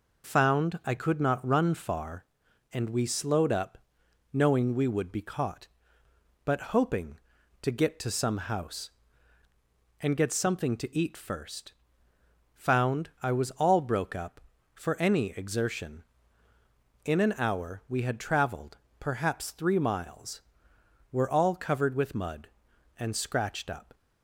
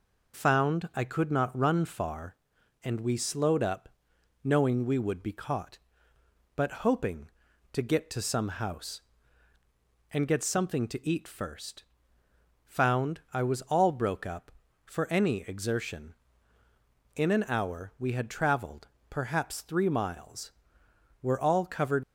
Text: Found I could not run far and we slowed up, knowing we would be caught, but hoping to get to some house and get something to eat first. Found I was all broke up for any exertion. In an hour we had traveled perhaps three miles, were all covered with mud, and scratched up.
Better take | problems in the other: first | pauses between "traveled" and "perhaps"; slight; at 18.8 s; 0.22 s long; slight in the first // stops before "with mud and scratched up"; at 22.0 s

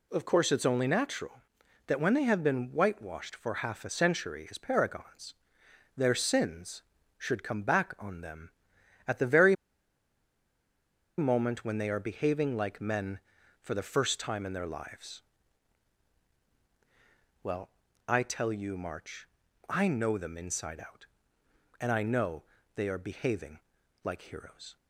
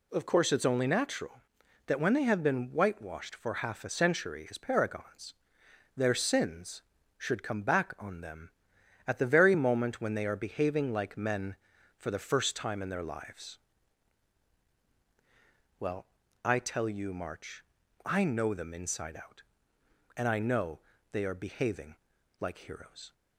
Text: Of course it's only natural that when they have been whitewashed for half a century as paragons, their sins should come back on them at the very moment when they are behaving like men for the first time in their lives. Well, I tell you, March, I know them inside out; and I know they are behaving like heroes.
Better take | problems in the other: second | pauses between "very" and "moment"; strong; at 9.5 s; 1.6 s long // pauses between "know" and "they"; slight; at 22.4 s; 0.32 s long; slight in the second // pauses between "behaving" and "like"; at 23.6 s; 0.44 s long; also in the second

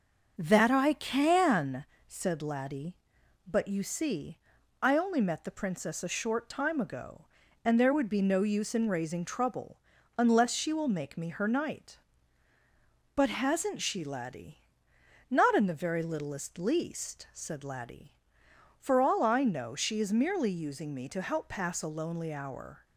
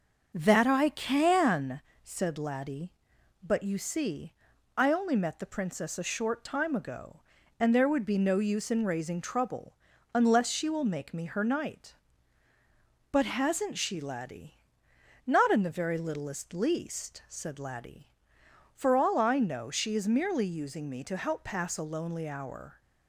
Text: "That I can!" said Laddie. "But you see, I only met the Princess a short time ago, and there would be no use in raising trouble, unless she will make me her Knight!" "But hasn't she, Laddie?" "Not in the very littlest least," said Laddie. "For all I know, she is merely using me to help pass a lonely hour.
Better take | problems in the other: neither | starts louder than the rest; the same in both

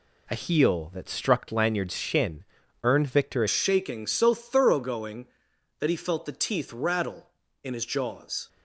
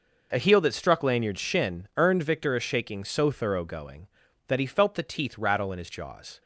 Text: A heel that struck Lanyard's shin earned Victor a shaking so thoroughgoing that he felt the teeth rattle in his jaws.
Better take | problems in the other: second | pauses between "shin" and "earned"; at 2.4 s; 0.40 s long // changes voice at "shaking"; from 3.4 s on; 5.0 s long

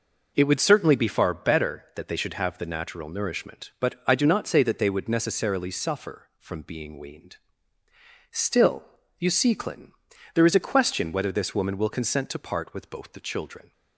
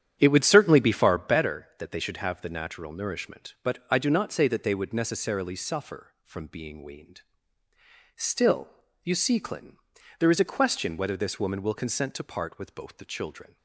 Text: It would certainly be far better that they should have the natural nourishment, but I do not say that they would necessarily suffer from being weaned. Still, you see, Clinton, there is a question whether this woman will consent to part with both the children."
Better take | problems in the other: first | starts louder than the rest; strong; until 1.4 s; 9 dB

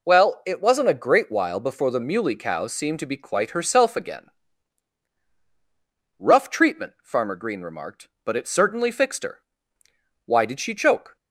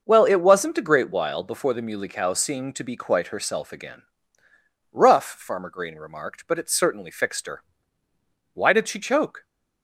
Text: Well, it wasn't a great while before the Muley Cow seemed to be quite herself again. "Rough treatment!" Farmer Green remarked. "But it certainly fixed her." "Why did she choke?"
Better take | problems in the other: first | skips "treatment"; at 5.2 s

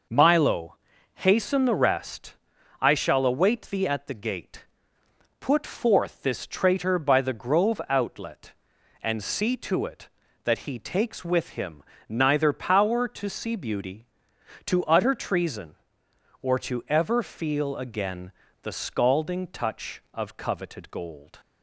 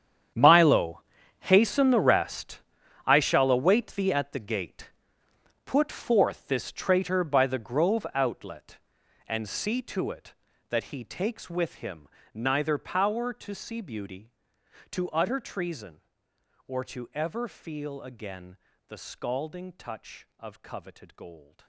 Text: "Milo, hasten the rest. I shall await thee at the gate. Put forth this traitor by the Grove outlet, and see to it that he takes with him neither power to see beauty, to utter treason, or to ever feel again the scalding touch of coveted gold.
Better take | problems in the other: first | gets quieter; strong; throughout; 17.5 dB // pauses between "him" and "neither"; slight; at 12.0 s; 0.26 s long; slight in the first // pauses between "again" and "the"; slight; at 18.5 s; 0.30 s long; slight in the first

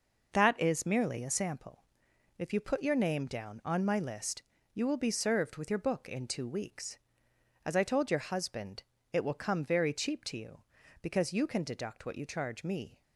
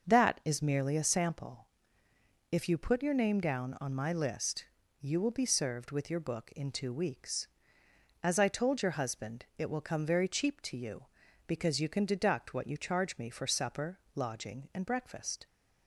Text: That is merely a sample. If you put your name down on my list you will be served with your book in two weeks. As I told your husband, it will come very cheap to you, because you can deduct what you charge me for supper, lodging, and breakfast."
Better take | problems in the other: second | pauses between "list" and "you"; slight; at 4.4 s; 0.32 s long; slight in the second // stops before "for supper lodging and breakfast"; at 13.0 s

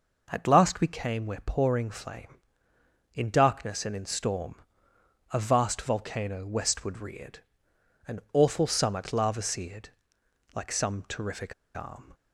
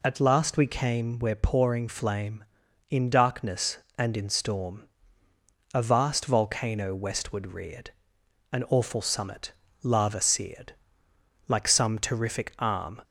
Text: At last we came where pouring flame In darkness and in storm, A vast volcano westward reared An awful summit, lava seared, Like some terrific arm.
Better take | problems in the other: second | pauses between "reared" and "An"; noticeable; at 7.3 s; 0.68 s long; noticeable in the second // pauses between "terrific" and "arm"; slight; at 11.5 s; 0.22 s long

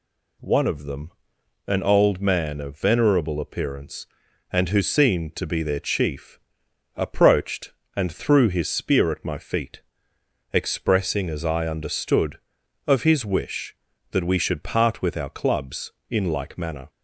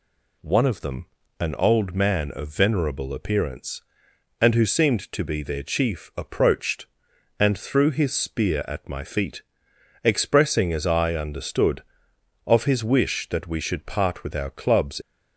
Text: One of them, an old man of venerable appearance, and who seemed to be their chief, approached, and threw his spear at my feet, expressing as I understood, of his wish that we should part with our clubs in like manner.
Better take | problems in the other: first | stops before "in like manner"; at 15.0 s

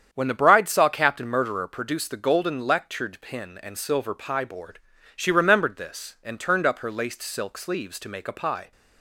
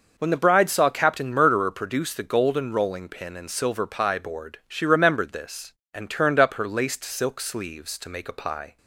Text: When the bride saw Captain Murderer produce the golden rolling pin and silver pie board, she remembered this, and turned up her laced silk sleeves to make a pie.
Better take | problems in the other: second | starts louder than the rest; strong; until 1.1 s; 8 dB // says "lectured" for "rolling"; at 2.6 s

